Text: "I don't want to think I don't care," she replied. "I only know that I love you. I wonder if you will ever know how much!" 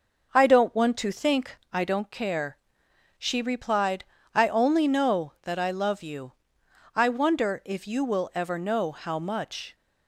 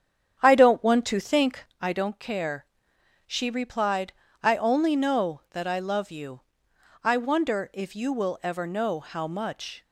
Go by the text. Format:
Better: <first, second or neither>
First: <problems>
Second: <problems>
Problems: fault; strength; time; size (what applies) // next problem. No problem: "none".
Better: first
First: pauses between "think" and "I"; slight; at 1.5 s; 0.16 s long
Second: starts louder than the rest; strong; until 1.7 s; 8.5 dB // pauses between "think" and "I"; slight; at 1.6 s; 0.16 s long